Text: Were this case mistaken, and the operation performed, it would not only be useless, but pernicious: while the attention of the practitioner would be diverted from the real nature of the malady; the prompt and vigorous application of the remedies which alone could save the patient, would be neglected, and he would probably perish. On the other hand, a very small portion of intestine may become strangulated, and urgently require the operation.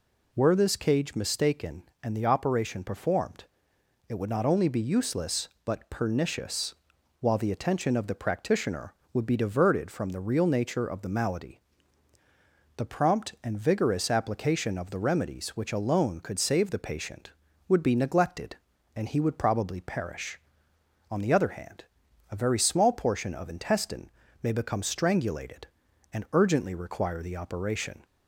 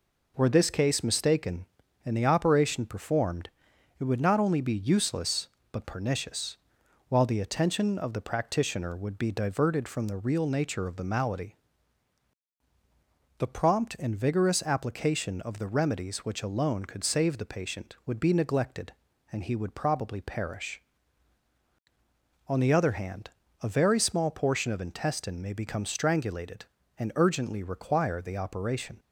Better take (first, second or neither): second